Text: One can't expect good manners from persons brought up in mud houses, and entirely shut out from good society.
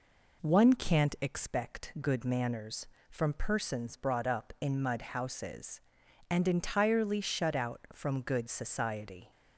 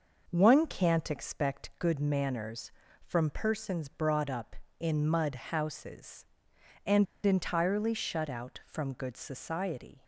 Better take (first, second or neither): first